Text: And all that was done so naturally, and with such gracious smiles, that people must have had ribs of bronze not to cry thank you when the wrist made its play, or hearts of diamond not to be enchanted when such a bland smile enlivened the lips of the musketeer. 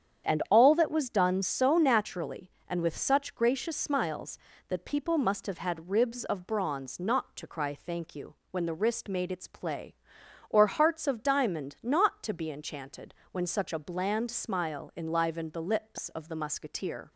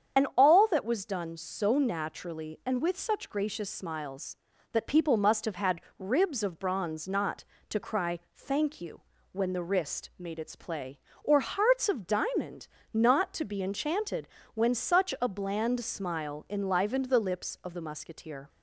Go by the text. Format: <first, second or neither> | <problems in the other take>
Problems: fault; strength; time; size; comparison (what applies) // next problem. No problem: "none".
first | loses the start of "And"; at 0.1 s; 45 ms // starts louder than the rest; strong; until 1.2 s; 8 dB; strong in the first // pauses between "had" and "ribs"; slight; at 5.8 s; 0.18 s long // pauses between "cry" and "thank"; slight; at 8.1 s; 0.16 s long // pauses between "you" and "when"; slight; at 9.0 s; 0.32 s long; slight in the first // pauses between "diamond" and "not"; slight; at 12.6 s; 0.24 s long // pauses between "enchanted" and "when"; slight; at 14.2 s; 0.26 s long; slight in the first